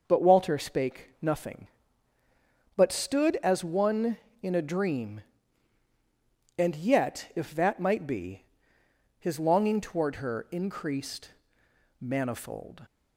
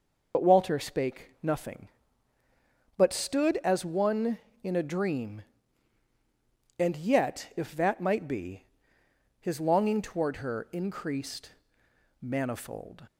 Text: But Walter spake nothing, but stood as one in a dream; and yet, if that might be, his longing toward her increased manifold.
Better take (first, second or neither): first